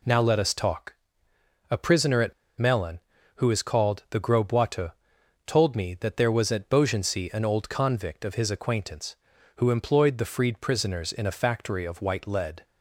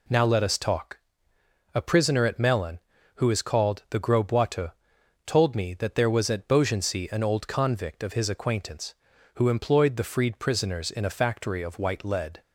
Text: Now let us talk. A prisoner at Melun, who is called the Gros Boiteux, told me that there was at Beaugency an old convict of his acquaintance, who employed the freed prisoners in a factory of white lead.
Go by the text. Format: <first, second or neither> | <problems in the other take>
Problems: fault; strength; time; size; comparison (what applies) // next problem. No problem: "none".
second | pauses between "at" and "Melun"; slight; at 2.3 s; 0.25 s long